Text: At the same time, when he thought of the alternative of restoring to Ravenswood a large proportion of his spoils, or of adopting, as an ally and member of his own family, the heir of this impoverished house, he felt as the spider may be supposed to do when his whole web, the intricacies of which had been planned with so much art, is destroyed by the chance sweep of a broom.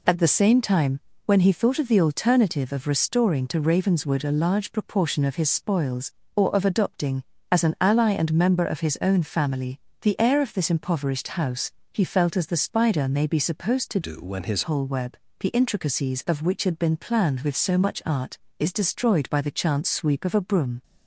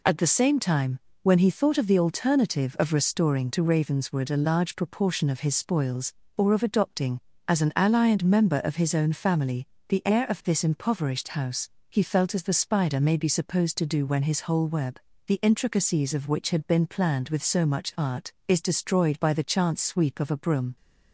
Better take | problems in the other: second | changes voice from "do" to "his"; from 14.0 to 14.6 s; 0.6 s long

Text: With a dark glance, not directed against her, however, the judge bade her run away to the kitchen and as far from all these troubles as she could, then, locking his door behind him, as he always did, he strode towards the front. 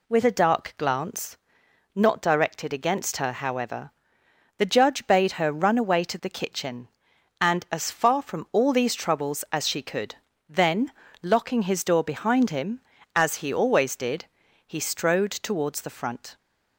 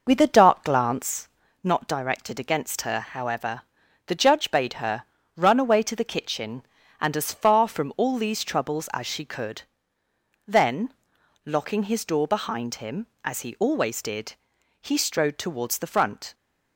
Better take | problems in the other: first | starts louder than the rest; noticeable; until 1.2 s; 5.5 dB // pauses between "her" and "run"; slight; at 5.0 s; 0.32 s long

